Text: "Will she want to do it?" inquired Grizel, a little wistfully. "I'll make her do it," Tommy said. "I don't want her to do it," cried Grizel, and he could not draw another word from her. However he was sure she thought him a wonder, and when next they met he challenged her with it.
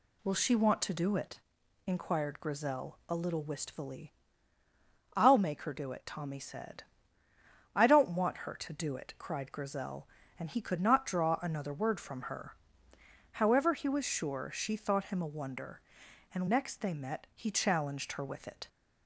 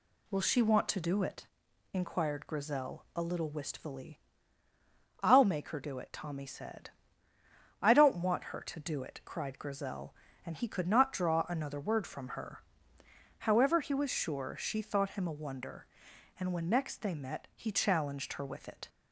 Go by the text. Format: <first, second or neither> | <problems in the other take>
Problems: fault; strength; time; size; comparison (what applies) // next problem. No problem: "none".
second | skips "when"; at 16.4 s